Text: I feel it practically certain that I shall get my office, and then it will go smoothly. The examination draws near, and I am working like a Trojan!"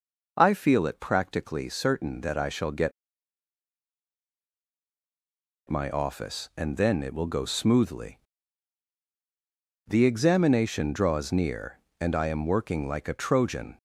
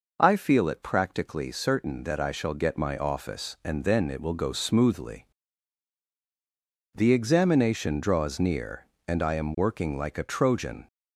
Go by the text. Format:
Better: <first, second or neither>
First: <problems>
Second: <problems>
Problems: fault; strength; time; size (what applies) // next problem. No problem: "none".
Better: second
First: pauses between "get" and "my"; strong; at 2.9 s; 2.7 s long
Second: none